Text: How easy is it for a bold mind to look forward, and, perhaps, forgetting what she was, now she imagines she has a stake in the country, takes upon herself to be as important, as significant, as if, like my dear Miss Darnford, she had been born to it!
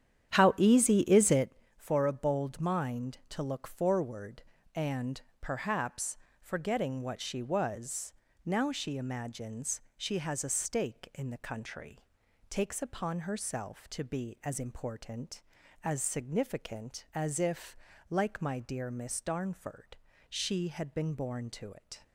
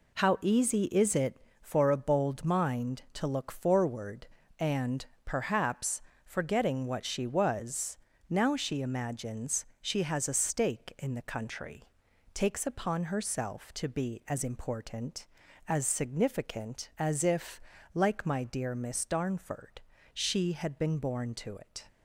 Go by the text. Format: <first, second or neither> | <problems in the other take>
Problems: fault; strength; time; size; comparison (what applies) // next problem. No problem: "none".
second | starts louder than the rest; strong; until 1.5 s; 10 dB // pauses between "imagines" and "she"; slight; at 9.8 s; 0.16 s long; slight in the second